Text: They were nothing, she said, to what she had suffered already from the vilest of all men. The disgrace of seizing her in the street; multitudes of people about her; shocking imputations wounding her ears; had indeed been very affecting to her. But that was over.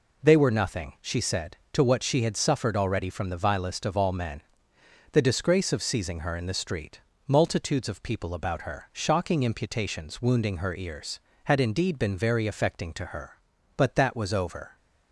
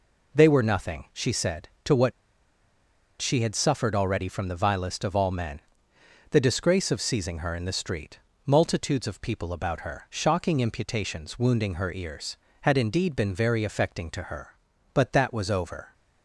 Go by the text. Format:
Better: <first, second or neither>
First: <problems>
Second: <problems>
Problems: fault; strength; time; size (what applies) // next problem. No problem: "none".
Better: first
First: none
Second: pauses between "what" and "she"; at 2.1 s; 1.0 s long